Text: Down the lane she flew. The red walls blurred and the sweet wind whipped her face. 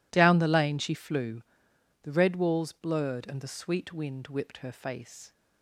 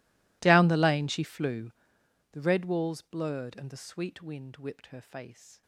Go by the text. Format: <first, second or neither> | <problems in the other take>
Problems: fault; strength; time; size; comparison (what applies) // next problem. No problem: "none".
first | gets quieter; strong; throughout; 25.5 dB